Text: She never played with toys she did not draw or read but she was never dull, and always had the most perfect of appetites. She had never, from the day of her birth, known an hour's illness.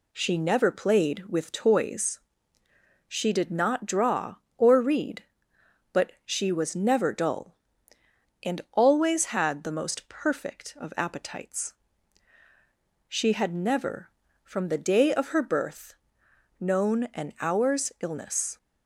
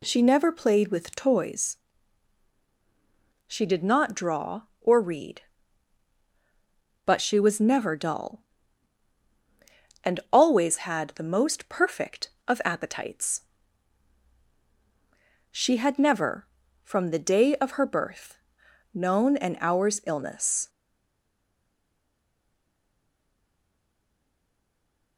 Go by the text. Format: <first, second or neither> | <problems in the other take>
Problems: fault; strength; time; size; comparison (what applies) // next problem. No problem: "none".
first | pauses between "toys" and "she"; strong; at 1.7 s; 1.7 s long; noticeable in the first // stays silent after the last word; strong; from 20.6 s on; 4.5 s long